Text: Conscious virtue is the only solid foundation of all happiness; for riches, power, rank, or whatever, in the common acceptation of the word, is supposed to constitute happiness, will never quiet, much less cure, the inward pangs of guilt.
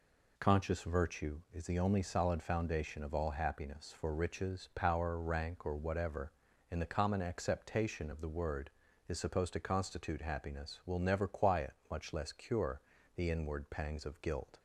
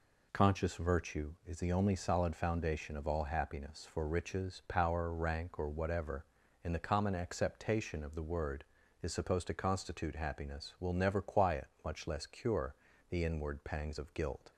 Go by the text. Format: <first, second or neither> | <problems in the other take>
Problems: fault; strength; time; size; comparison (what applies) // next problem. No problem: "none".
neither | none